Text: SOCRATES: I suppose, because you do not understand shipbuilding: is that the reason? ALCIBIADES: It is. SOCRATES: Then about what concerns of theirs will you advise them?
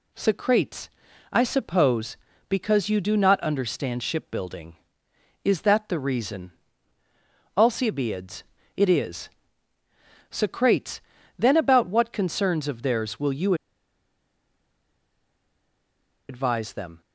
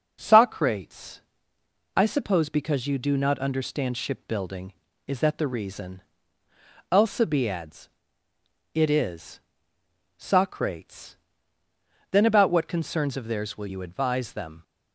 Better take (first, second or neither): second